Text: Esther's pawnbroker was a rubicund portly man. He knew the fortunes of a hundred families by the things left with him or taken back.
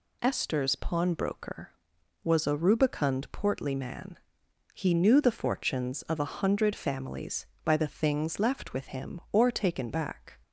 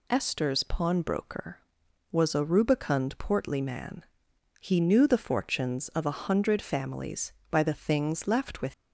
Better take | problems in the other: first | stops before "him or taken back"; at 8.7 s

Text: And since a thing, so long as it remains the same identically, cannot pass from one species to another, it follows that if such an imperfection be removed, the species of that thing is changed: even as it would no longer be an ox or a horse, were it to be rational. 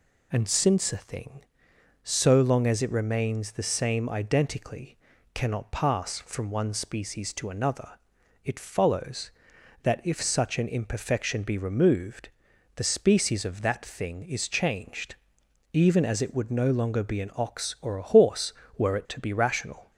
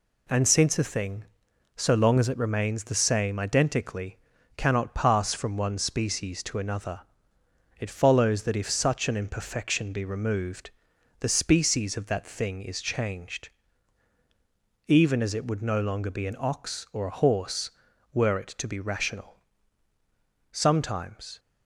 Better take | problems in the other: first | goes on to say "Sometimes"; noticeable; from 20.5 s on; 0.88 s long

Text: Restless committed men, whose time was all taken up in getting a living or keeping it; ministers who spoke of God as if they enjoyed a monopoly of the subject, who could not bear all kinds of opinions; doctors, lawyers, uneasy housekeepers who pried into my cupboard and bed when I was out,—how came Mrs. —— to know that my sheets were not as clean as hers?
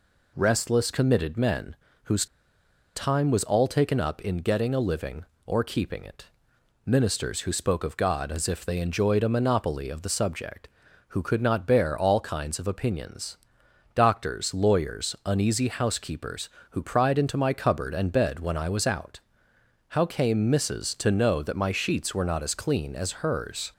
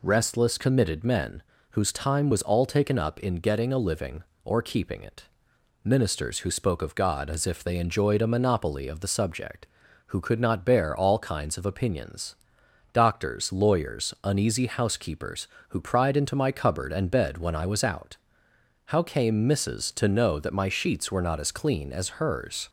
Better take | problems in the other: second | pauses between "whose" and "time"; noticeable; at 2.2 s; 0.69 s long

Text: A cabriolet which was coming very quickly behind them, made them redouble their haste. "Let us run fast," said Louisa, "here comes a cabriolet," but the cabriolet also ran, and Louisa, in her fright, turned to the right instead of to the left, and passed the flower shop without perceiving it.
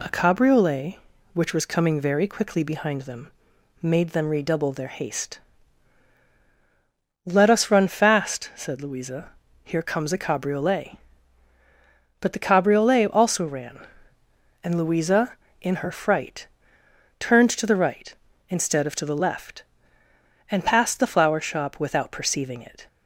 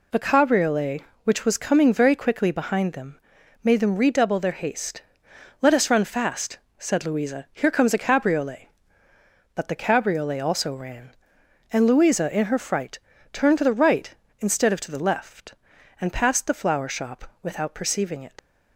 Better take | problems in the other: first | leaves "it" unfinished; at 18.3 s; 85 ms

